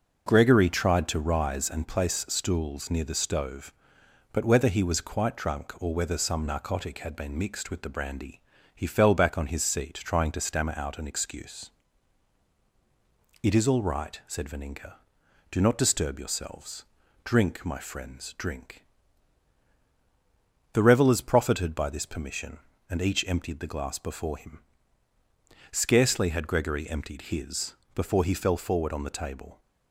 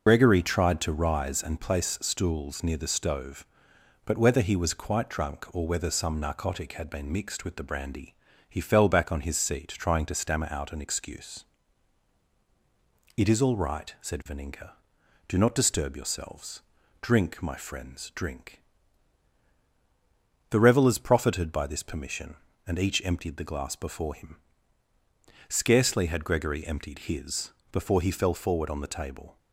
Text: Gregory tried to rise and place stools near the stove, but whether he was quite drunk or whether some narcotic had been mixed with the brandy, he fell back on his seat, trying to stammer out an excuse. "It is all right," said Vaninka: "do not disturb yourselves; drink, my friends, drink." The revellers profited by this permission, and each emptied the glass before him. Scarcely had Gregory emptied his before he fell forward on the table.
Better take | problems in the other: first | loses the start of "Gregory"; at 0.0 s; 75 ms // pauses between "his" and "before"; slight; at 27.5 s; 0.18 s long; slight in the first

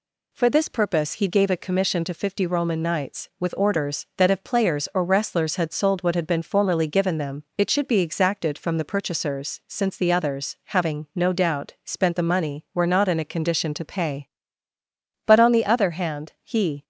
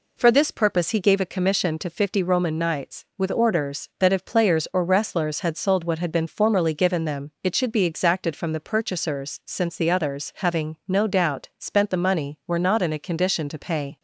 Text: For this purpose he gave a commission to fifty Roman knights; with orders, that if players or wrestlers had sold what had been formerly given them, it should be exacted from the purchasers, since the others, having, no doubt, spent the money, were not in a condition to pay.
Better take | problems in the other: second | goes on to say "But on the other hand he"; from 15.2 s on; 1.5 s long

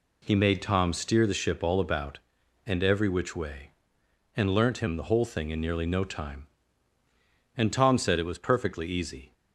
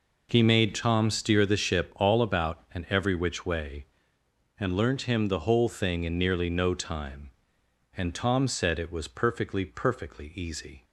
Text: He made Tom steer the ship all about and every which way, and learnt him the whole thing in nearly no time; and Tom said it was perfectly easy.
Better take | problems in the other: first | says "perfectly" twice; at 9.6 s

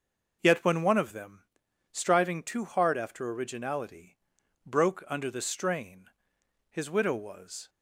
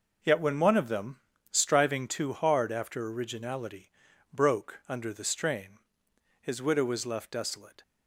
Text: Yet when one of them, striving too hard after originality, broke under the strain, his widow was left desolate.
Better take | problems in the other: second | stops before "left desolate"; at 7.6 s

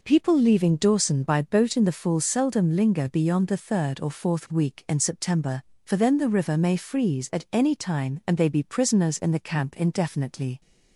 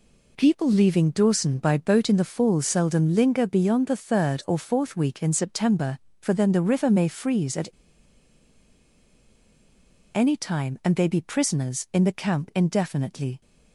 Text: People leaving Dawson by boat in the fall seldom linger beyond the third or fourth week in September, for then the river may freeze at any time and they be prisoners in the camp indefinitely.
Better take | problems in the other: first | pauses between "at" and "any"; strong; at 7.6 s; 2.4 s long

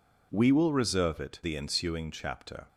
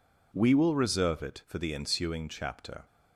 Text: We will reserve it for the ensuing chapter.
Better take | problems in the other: second | skips "for"; at 1.4 s

